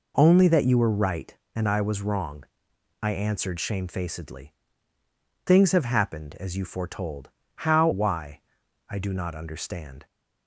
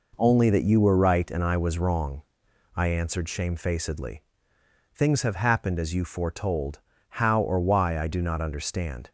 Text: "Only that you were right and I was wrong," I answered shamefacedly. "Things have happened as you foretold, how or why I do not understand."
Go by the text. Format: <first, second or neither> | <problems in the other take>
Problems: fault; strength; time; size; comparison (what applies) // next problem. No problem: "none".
second | skips "or"; at 7.9 s // pauses between "why" and "I"; noticeable; at 8.4 s; 0.48 s long